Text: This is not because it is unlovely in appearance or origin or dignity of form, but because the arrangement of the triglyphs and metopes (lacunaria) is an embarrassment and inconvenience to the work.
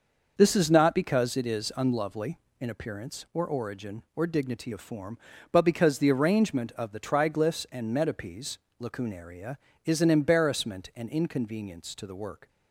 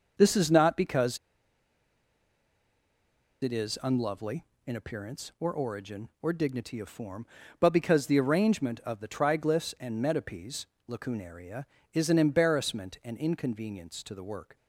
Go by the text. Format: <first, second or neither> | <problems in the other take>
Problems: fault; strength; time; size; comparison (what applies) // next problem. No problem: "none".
first | starts louder than the rest; noticeable; until 1.1 s; 6 dB; noticeable in the first // pauses between "because" and "it"; strong; at 1.1 s; 2.2 s long